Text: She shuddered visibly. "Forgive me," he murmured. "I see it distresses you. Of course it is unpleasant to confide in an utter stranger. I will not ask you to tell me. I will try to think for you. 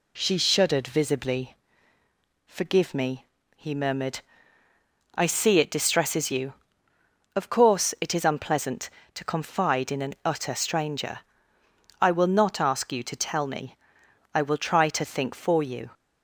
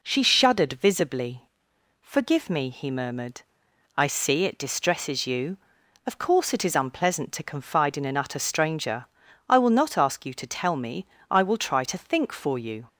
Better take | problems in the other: neither | none

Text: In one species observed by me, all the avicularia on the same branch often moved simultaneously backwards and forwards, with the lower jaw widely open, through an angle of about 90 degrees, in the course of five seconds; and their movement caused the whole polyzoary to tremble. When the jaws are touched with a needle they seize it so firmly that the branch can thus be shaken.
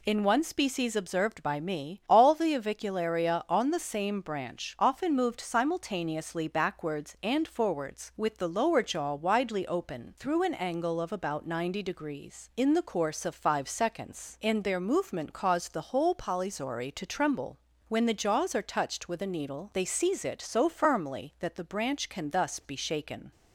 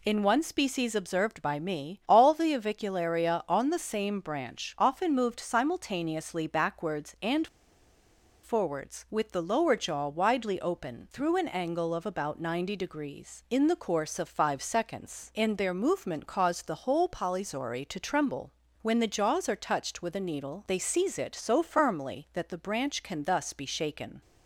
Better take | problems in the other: first | pauses between "and" and "forwards"; noticeable; at 7.4 s; 0.97 s long

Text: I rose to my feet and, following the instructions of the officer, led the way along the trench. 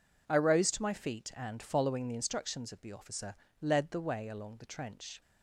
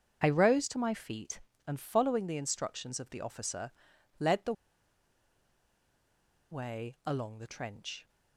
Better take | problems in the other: first | starts louder than the rest; until 1.2 s; 6.5 dB // pauses between "the" and "way"; strong; at 4.5 s; 1.9 s long

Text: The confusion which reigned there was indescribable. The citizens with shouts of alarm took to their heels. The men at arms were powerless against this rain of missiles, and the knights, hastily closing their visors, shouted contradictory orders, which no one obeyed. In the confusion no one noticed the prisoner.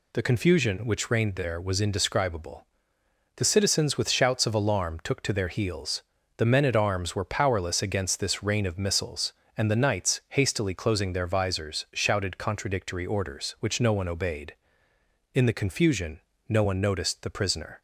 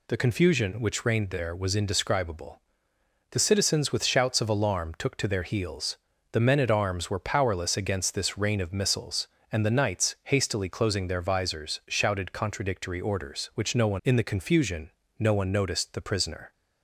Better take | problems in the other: first | skips "obeyed"; at 14.0 s // pauses between "confusion" and "no"; slight; at 14.8 s; 0.28 s long; slight in the first

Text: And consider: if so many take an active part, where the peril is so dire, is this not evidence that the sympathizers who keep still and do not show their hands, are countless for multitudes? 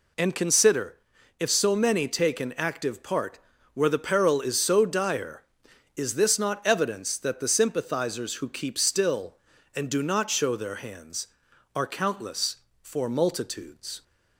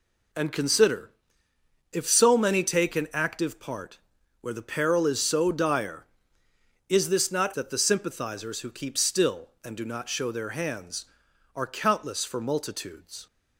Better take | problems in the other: first | skips "evidence"; at 7.5 s

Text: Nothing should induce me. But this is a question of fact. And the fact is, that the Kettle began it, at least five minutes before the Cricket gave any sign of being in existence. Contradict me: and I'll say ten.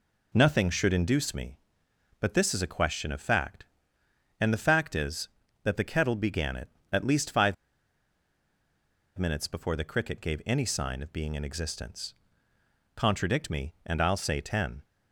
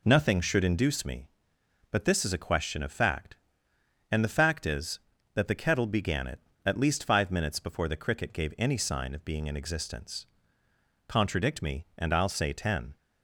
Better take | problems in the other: second | pauses between "five" and "minutes"; strong; at 7.5 s; 1.6 s long

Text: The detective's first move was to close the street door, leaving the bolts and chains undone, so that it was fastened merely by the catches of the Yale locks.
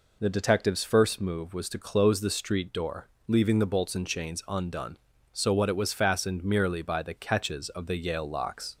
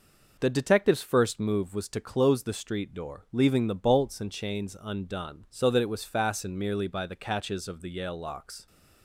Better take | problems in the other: second | says "what" for "that"; at 5.5 s

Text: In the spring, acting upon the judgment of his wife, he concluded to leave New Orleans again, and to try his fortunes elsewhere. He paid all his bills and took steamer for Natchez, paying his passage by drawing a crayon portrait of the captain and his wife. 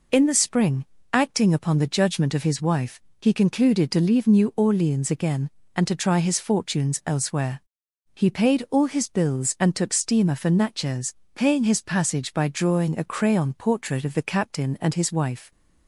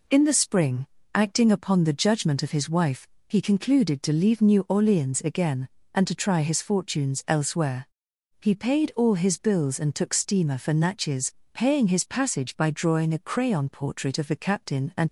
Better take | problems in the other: first | stops before "his wife"; at 15.0 s

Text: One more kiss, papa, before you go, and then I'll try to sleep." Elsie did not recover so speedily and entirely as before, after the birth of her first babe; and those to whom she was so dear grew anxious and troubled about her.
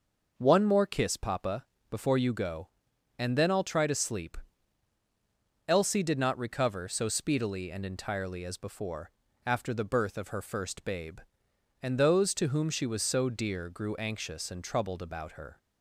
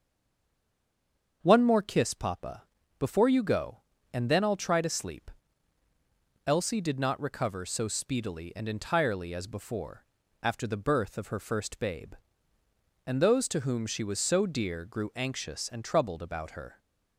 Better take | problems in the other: first | stays silent before the first word; noticeable; until 1.4 s; 1.4 s long // starts louder than the rest; until 2.4 s; 7 dB

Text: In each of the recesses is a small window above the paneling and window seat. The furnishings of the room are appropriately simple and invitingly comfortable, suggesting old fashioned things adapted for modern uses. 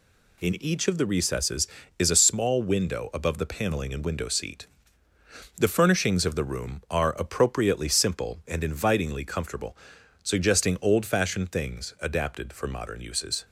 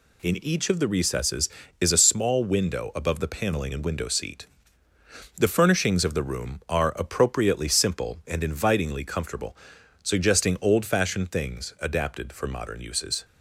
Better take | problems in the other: neither | none

